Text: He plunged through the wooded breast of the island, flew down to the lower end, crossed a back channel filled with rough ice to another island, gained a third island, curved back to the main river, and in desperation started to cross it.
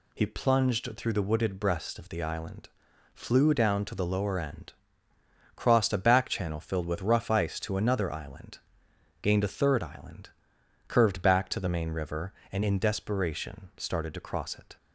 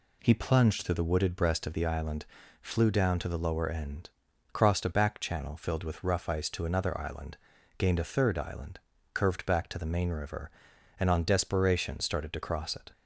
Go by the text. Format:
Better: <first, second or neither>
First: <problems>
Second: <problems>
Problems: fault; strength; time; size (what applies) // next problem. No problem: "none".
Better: first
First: none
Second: says "on" for "in"; at 11.1 s